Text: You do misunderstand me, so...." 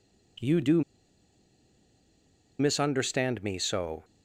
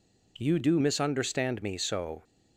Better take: second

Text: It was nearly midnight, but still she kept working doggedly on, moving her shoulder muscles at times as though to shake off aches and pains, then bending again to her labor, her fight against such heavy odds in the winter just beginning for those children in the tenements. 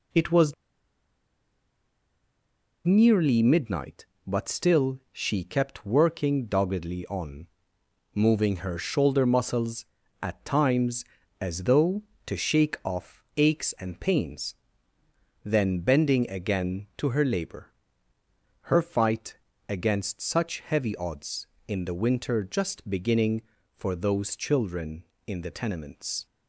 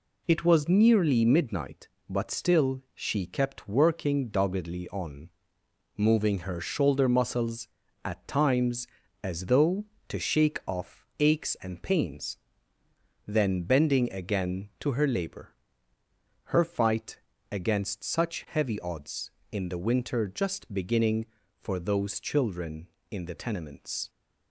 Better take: second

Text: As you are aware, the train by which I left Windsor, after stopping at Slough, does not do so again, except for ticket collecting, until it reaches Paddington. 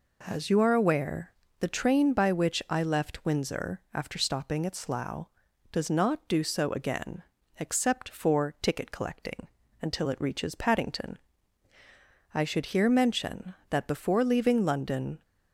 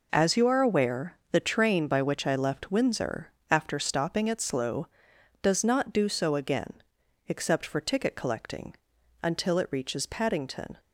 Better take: second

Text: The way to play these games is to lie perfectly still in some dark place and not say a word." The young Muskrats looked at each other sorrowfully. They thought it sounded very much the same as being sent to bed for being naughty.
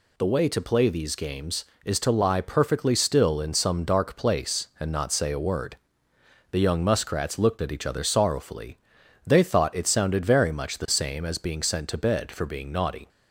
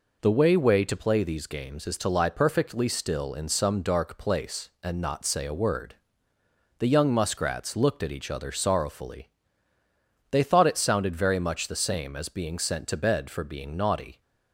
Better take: first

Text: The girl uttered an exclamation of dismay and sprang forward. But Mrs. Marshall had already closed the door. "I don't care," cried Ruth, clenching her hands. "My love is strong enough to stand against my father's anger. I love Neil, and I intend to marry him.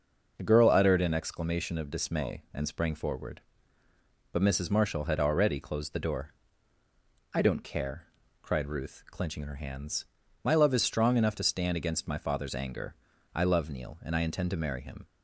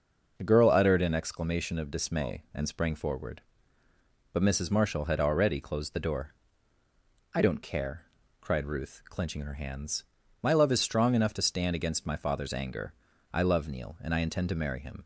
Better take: neither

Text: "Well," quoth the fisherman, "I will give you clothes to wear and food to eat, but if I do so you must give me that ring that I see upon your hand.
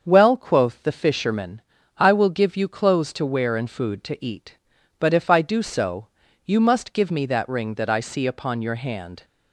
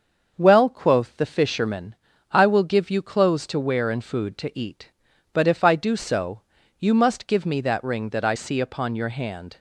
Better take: neither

